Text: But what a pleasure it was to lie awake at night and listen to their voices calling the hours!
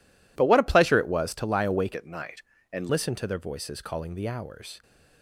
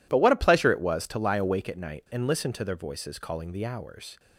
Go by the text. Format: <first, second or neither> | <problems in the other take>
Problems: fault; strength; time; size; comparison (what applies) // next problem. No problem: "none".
second | changes voice from "at" to "and"; from 1.9 to 2.8 s; 0.9 s long